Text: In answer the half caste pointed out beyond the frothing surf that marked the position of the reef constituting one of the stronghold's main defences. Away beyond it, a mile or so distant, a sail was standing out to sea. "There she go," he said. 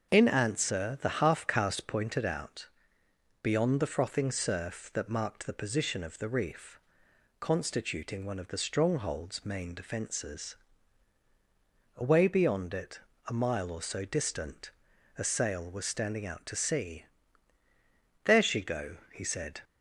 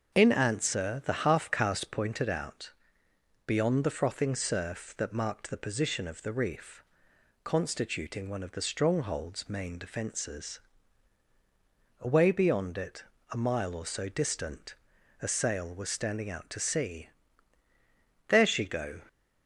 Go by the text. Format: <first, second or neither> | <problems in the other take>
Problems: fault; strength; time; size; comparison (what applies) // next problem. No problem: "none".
first | starts louder than the rest; until 1.2 s; 6.5 dB; also in the first // pauses between "out" and "beyond"; noticeable; at 2.7 s; 0.74 s long; noticeable in the first // pauses between "reef" and "constituting"; noticeable; at 6.8 s; 0.62 s long; noticeable in the first // stops before "he said"; at 19.0 s